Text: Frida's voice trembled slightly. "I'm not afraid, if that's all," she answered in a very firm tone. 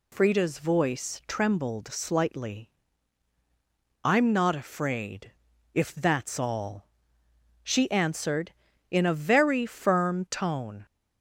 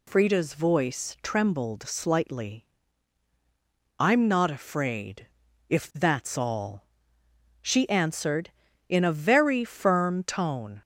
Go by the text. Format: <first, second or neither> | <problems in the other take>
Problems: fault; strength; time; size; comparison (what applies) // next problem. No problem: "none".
neither | none